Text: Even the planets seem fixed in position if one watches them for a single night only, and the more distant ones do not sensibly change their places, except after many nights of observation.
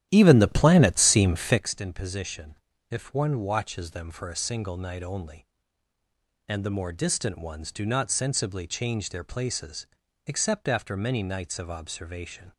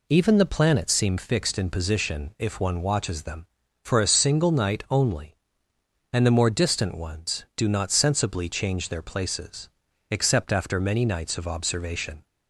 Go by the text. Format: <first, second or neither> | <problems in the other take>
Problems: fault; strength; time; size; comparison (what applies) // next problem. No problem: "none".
second | starts louder than the rest; strong; until 1.7 s; 11.5 dB // pauses between "position" and "if"; slight; at 2.5 s; 0.34 s long